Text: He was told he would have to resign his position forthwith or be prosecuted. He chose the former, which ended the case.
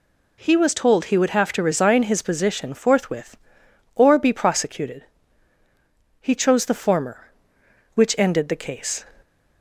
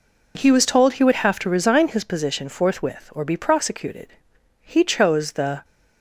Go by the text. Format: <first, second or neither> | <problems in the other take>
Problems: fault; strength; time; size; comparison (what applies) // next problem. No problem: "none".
first | stops before "former which ended the case"; at 5.6 s